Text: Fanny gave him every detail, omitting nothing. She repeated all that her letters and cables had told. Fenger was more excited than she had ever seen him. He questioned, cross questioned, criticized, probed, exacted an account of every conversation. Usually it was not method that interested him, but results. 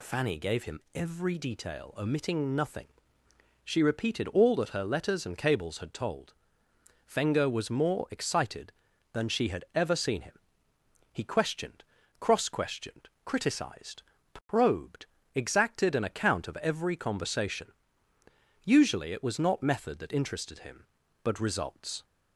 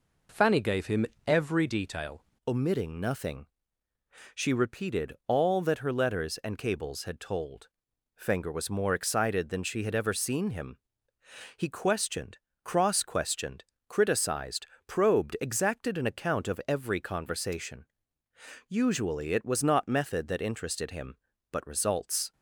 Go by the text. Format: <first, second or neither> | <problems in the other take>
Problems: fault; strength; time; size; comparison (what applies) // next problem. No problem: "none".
first | pauses between "him" and "every"; slight; at 1.0 s; 0.20 s long // changes voice at "omitting"; from 2.4 s on; 19.9 s long